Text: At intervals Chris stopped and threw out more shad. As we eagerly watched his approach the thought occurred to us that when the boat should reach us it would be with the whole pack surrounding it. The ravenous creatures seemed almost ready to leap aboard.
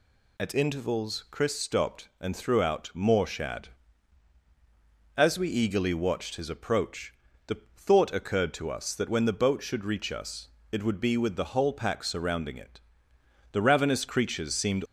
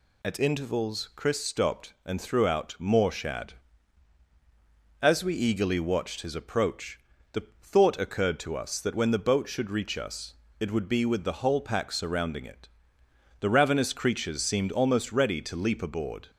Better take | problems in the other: second | pauses between "approach" and "the"; slight; at 7.1 s; 0.34 s long; slight in the second // pauses between "the" and "thought"; slight; at 7.5 s; 0.18 s long; slight in the second // pauses between "us" and "it"; slight; at 10.4 s; 0.24 s long; slight in the second // stops before "almost ready to leap aboard"; at 14.8 s

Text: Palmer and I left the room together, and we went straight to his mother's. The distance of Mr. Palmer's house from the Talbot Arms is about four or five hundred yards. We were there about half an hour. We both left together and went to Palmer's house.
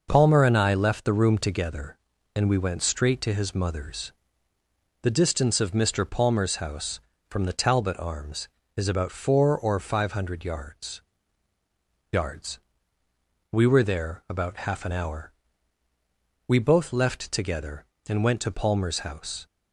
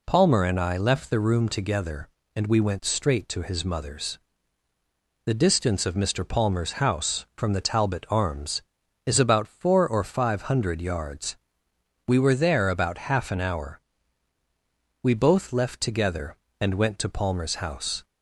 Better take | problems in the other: second | says "yards" twice; at 12.1 s

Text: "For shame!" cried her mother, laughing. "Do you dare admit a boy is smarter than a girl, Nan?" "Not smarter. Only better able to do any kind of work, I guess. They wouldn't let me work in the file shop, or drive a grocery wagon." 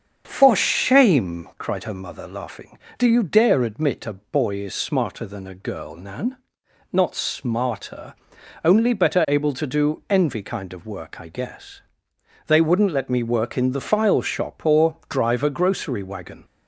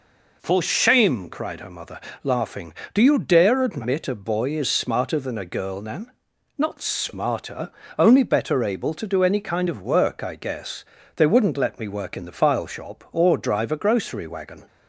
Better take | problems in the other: second | starts louder than the rest; strong; until 1.2 s; 7.5 dB // says "envy" for "any"; at 10.0 s

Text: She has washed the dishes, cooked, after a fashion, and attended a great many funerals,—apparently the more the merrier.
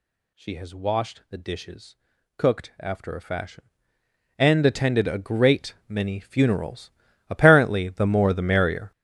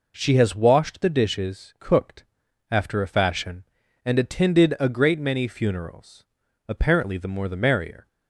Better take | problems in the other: second | gets louder; strong; throughout; 12 dB

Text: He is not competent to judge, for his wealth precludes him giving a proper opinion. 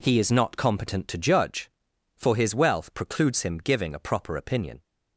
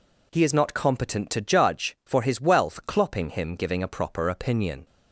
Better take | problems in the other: first | says "clopping" for "precludes"; at 2.8 s

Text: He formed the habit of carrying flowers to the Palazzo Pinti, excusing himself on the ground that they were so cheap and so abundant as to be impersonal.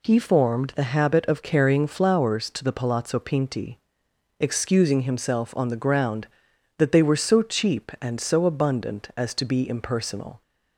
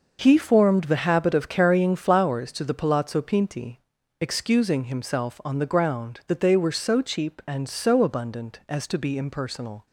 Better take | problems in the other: neither | none

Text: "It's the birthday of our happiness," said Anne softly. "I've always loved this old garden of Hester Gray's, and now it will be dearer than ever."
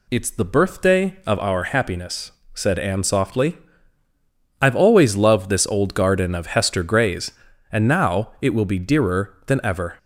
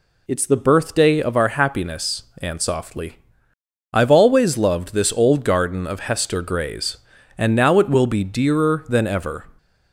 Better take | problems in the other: first | skips "said"; at 2.3 s

